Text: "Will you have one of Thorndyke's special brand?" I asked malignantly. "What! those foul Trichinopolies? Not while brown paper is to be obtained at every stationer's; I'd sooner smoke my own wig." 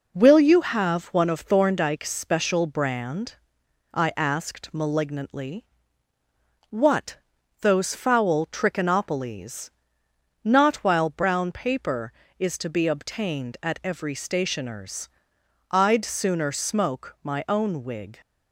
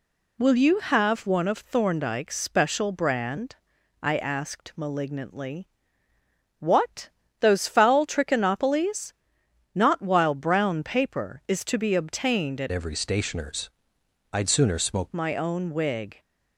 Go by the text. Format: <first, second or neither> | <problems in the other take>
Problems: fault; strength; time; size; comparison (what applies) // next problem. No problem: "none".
first | changes voice from "every" to "smoke"; from 12.6 to 15.0 s; 2.4 s long